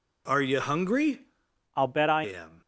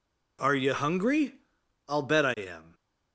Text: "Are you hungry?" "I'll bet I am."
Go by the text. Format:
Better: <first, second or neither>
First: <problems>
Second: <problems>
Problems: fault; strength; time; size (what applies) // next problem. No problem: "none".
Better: second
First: changes voice from "I'll" to "I"; from 1.7 to 2.2 s; 0.5 s long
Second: none